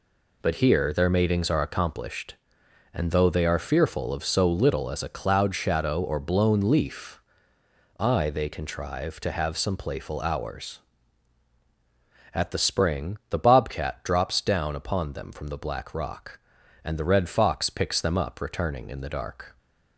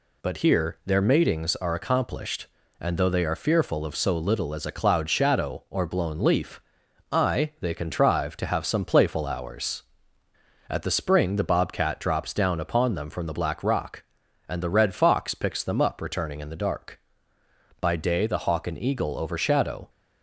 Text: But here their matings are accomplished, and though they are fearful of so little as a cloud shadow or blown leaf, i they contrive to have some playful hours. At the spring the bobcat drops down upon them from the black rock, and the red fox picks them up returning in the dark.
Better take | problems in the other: first | goes on to say "By day the hawk and eagle overshadow"; strong; from 17.7 s on; 2.1 s long

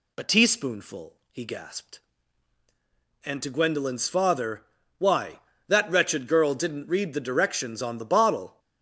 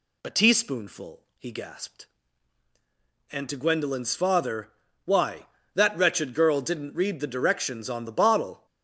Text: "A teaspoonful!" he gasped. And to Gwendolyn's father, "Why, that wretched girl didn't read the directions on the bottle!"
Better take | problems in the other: neither | none

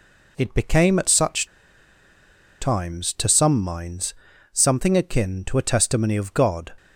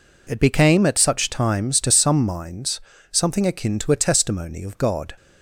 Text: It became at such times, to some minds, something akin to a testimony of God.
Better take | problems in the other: second | pauses between "such" and "times"; at 1.4 s; 1.1 s long

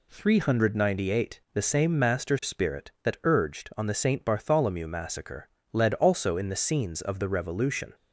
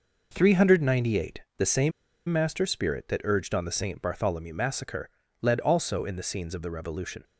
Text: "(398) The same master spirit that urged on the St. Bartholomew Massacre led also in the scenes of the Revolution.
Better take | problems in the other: first | pauses between "same" and "master"; at 1.9 s; 0.37 s long // pauses between "Massacre" and "led"; slight; at 5.0 s; 0.34 s long; slight in the first

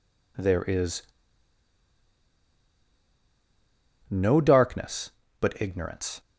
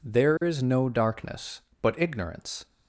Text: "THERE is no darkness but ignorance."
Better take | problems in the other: second | pauses between "is" and "no"; strong; at 1.0 s; 3.0 s long

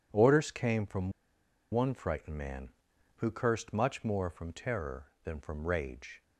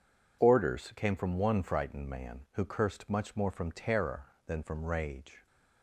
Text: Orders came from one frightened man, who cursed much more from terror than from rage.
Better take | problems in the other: second | pauses between "from" and "one"; noticeable; at 1.1 s; 0.60 s long

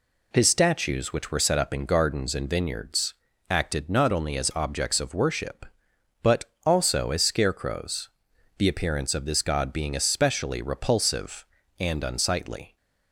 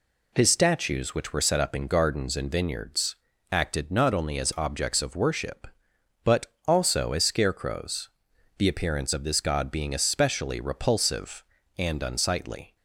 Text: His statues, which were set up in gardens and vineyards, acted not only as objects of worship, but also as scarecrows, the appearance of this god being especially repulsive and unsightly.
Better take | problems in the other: neither | pauses between "but" and "also"; slight; the same in both

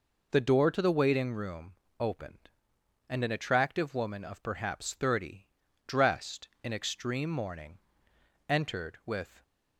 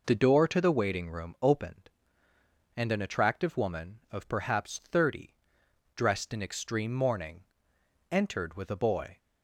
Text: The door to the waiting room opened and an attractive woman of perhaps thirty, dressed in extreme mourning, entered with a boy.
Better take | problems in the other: second | pauses between "room" and "opened"; slight; at 1.7 s; 0.26 s long // stops before "a boy"; at 9.4 s

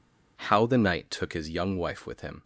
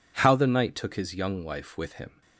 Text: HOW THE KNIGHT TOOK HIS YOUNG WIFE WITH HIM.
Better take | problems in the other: neither | none

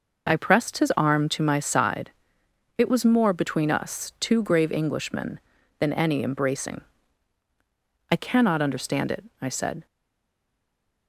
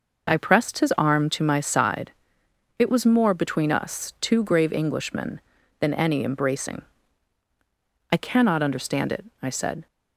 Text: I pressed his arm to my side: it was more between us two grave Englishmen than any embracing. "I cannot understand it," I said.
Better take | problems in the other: second | stays silent after the last word; noticeable; from 9.8 s on; 1.2 s long

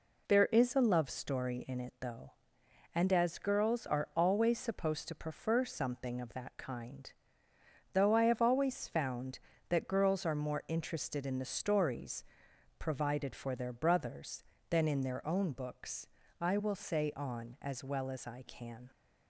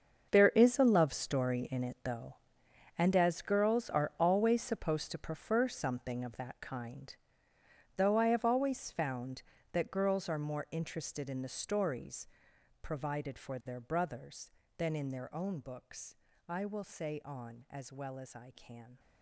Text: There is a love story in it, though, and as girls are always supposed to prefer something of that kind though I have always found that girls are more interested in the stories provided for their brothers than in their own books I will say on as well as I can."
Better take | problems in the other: first | gets quieter; strong; throughout; 14.5 dB // pauses between "kind" and "though"; noticeable; at 7.1 s; 0.82 s long; noticeable in the first // pauses between "stories" and "provided"; noticeable; at 12.2 s; 0.52 s long; noticeable in the first // pauses between "books" and "I"; slight; at 16.1 s; 0.34 s long; slight in the first

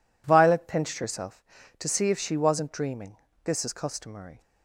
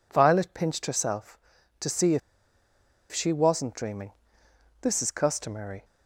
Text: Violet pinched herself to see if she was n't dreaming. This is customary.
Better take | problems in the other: first | pauses between "if" and "she"; noticeable; at 2.2 s; 0.92 s long

